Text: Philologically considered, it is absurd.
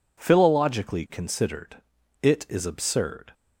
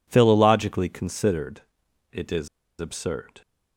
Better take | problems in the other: first | pauses between "is" and "absurd"; slight; at 2.4 s; 0.30 s long

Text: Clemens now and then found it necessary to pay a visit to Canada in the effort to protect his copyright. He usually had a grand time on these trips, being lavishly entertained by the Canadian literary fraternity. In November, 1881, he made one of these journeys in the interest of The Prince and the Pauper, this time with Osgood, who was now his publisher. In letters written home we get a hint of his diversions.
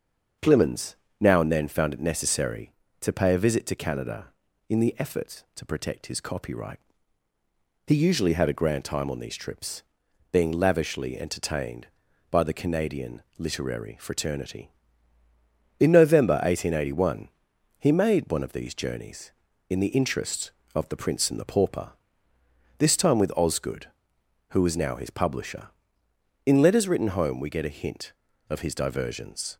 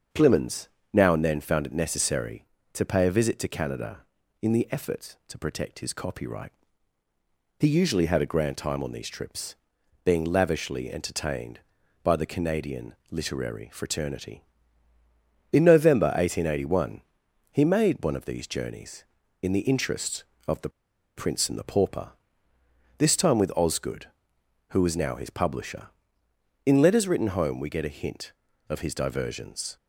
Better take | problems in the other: first | starts louder than the rest; until 1.3 s; 6.5 dB; also in the first // pauses between "Clemens" and "now"; slight; at 0.6 s; 0.26 s long; slight in the first // pauses between "The" and "Prince"; noticeable; at 20.6 s; 0.47 s long

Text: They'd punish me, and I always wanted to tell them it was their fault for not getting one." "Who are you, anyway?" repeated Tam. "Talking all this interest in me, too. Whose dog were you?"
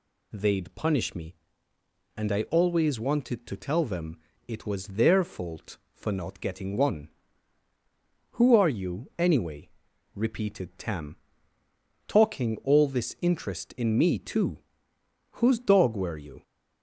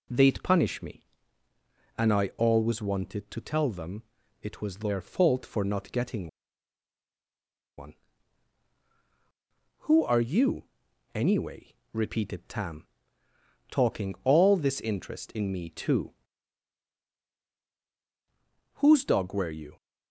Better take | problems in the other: first | pauses between "them" and "it"; at 4.0 s; 0.38 s long; slight in the first // pauses between "getting" and "one"; strong; at 6.2 s; 1.4 s long

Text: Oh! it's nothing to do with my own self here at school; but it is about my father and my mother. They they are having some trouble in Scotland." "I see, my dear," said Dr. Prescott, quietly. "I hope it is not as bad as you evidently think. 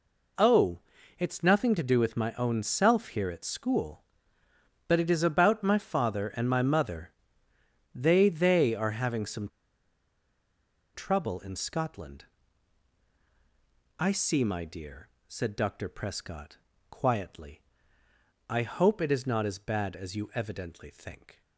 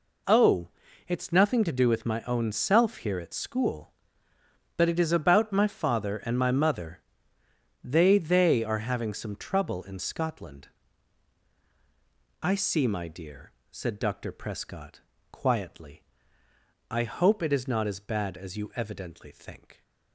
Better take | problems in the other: second | pauses between "some" and "trouble"; strong; at 9.4 s; 1.4 s long

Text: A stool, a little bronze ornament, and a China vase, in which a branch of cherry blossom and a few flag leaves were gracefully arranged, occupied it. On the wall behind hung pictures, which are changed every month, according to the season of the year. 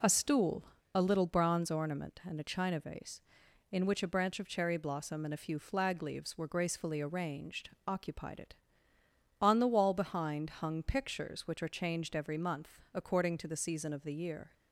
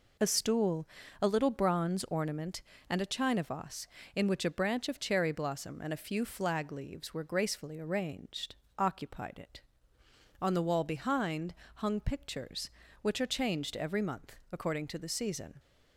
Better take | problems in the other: first | pauses between "behind" and "hung"; slight; at 11.5 s; 0.22 s long // stops before "of the year"; at 15.5 s

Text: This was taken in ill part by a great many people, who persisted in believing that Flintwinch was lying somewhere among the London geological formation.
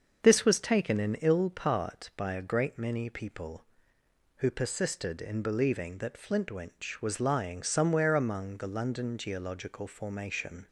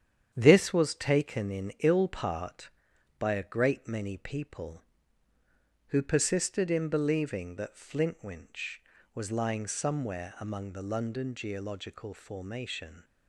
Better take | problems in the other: first | gets quieter; noticeable; throughout; 5 dB // starts louder than the rest; strong; until 1.3 s; 9 dB; also in the first

